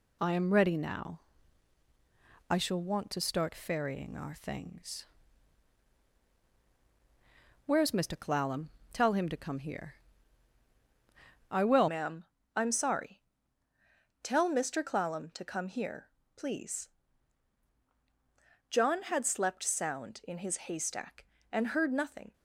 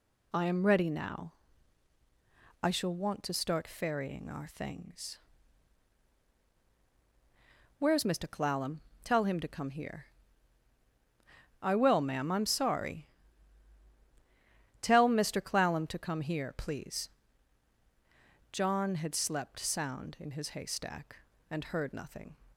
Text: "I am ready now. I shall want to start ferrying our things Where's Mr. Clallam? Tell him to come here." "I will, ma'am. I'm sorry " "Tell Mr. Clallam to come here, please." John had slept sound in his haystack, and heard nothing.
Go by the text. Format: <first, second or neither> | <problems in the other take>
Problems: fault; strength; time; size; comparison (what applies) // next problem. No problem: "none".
second | pauses between "things" and "Where's"; strong; at 5.0 s; 2.6 s long; strong in the second // changes voice at "ma'am"; from 11.8 s on; 10.5 s long